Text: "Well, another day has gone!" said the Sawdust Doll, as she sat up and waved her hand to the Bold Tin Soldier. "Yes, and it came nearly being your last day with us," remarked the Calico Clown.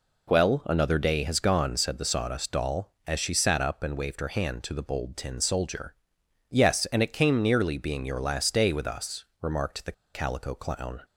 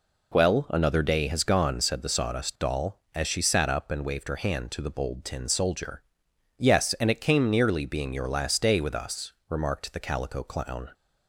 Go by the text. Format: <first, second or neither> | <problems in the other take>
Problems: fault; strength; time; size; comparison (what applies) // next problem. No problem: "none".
second | pauses between "the" and "Calico"; slight; at 9.9 s; 0.21 s long